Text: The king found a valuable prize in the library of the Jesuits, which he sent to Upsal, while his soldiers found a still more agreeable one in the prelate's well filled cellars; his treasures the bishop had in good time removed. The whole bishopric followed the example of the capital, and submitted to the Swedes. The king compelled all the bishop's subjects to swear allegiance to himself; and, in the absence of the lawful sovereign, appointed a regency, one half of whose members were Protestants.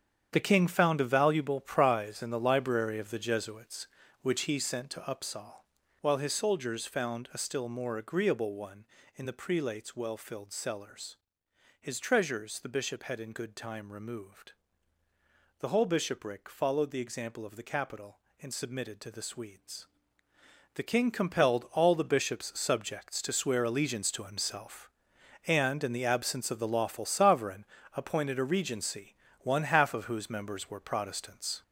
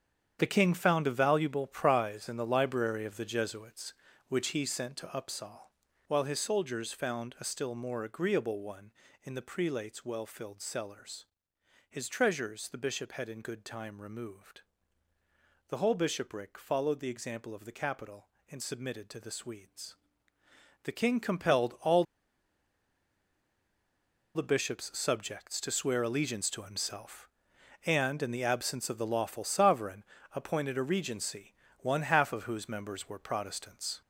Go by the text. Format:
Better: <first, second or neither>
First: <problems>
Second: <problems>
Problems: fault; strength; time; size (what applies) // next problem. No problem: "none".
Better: first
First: starts louder than the rest; strong; until 1.3 s; 8.5 dB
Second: starts louder than the rest; strong; until 1.4 s; 8.5 dB // pauses between "all" and "the"; strong; at 22.0 s; 2.3 s long